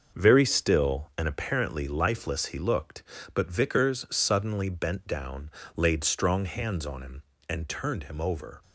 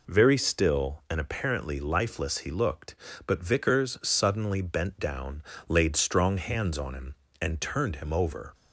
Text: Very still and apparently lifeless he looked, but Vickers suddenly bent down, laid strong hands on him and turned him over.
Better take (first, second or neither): second